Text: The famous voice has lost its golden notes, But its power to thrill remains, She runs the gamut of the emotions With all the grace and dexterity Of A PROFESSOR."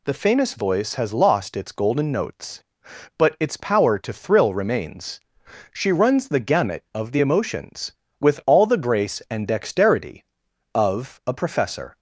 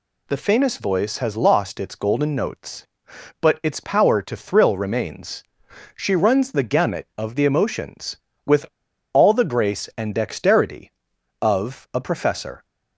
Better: first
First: none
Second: pauses between "With" and "all"; noticeable; at 8.6 s; 0.47 s long

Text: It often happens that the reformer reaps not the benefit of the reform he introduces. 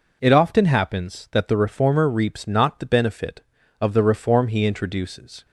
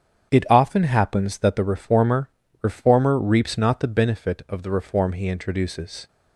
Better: first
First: none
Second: starts louder than the rest; strong; until 1.3 s; 8.5 dB // says "reformer" twice; at 2.6 s

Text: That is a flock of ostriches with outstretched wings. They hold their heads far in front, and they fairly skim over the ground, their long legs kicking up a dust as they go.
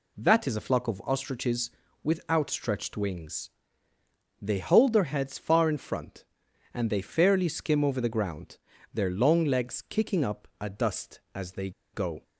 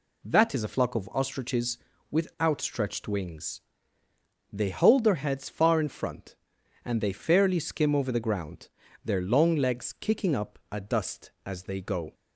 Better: second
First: pauses between "they" and "go"; slight; at 11.7 s; 0.23 s long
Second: none

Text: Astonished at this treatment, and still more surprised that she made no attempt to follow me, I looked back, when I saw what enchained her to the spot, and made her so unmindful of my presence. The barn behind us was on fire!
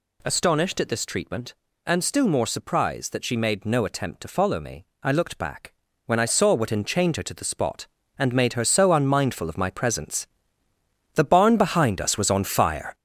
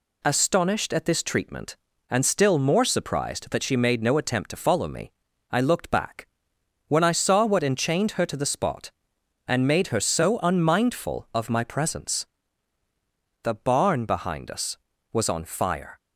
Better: second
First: gets louder; throughout; 7 dB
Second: none

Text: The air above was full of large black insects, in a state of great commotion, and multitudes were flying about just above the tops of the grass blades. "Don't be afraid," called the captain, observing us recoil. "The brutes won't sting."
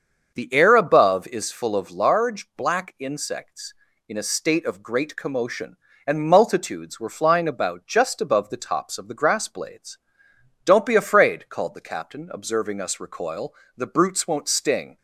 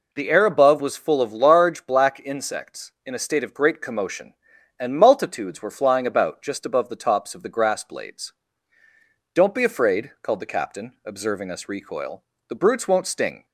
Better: second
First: starts louder than the rest; until 1.3 s; 6.5 dB // says "is" for "was"; at 1.2 s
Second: none

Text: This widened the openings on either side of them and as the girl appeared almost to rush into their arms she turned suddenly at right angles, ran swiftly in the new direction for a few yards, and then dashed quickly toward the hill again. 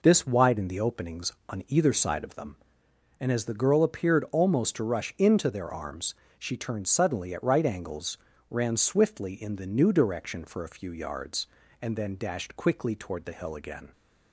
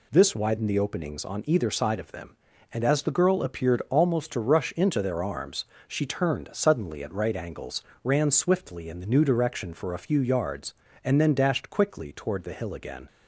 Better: neither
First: pauses between "arms" and "she"; slight; at 6.1 s; 0.24 s long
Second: pauses between "arms" and "she"; slight; at 5.6 s; 0.24 s long

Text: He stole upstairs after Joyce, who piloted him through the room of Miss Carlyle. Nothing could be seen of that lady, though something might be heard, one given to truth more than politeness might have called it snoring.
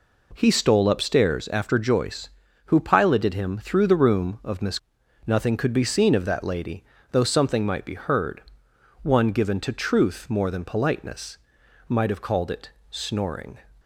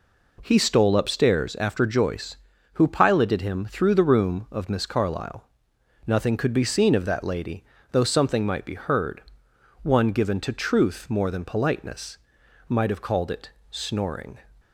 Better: second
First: skips "Carlyle"; at 5.0 s // pauses between "politeness" and "might"; noticeable; at 11.3 s; 0.50 s long // pauses between "it" and "snoring"; slight; at 12.6 s; 0.20 s long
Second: pauses between "politeness" and "might"; noticeable; at 12.1 s; 0.50 s long // pauses between "it" and "snoring"; slight; at 13.4 s; 0.20 s long

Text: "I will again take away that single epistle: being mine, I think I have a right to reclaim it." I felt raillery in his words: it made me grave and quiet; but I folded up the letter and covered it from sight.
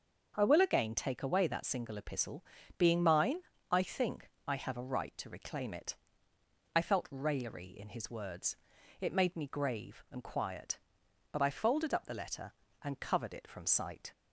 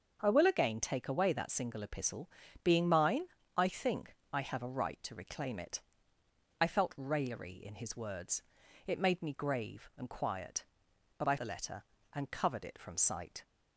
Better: first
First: starts louder than the rest; until 1.3 s; 6 dB // pauses between "think" and "I"; slight; at 4.2 s; 0.20 s long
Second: starts louder than the rest; until 1.2 s; 6.5 dB // pauses between "think" and "I"; slight; at 4.1 s; 0.20 s long // skips "folded up"; at 11.3 s

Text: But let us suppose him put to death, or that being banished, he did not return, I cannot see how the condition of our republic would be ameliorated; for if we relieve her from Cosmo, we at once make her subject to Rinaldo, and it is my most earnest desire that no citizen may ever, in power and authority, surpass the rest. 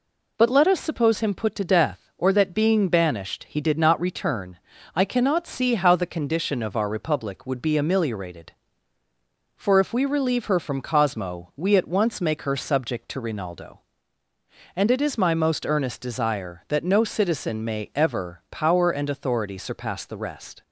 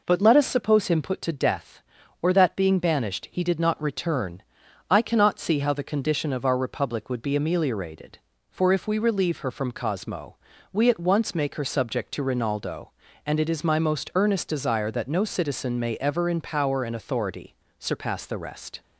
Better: second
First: skips "in"; at 18.4 s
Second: none

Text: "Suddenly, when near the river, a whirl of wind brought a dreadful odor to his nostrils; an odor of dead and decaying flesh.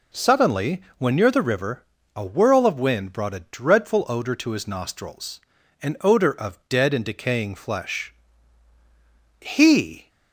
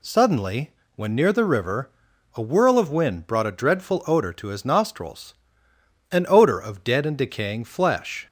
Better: second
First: goes on to say "He"; noticeable; from 9.4 s on; 0.68 s long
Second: none

